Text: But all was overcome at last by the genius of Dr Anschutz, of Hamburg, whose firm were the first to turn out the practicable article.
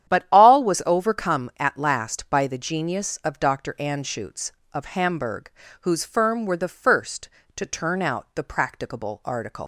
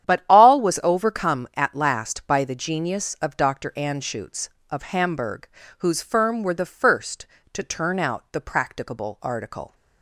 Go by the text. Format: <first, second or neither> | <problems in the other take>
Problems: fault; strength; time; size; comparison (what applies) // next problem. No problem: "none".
second | starts louder than the rest; strong; until 1.1 s; 10 dB; strong in the second // leaves "article" unfinished; at 9.6 s; 110 ms